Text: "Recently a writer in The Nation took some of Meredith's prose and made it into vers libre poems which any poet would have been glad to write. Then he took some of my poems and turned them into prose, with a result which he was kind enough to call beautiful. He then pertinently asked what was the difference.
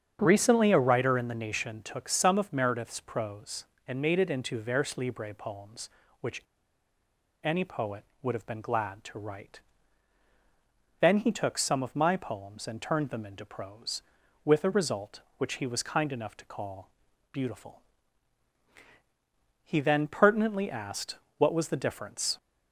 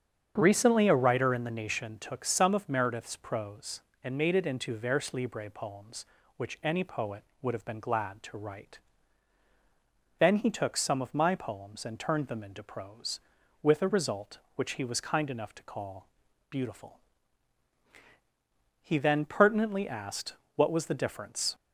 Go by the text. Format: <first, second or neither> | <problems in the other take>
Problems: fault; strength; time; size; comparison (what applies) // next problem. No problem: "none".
second | starts louder than the rest; strong; until 1.2 s; 8 dB; strong in the second // pauses between "which" and "any"; at 6.4 s; 1.0 s long // pauses between "call" and "beautiful"; at 16.9 s; 0.42 s long; also in the second // pauses between "asked" and "what"; slight; at 21.1 s; 0.22 s long; slight in the second